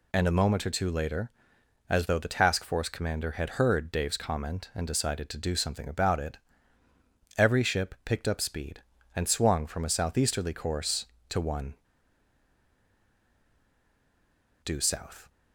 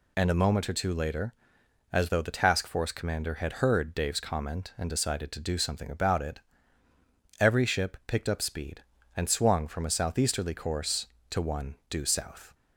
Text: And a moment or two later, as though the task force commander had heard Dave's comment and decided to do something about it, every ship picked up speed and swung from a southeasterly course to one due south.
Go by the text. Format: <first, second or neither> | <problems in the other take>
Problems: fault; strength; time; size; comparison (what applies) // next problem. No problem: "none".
second | pauses between "one" and "due"; strong; at 11.7 s; 2.8 s long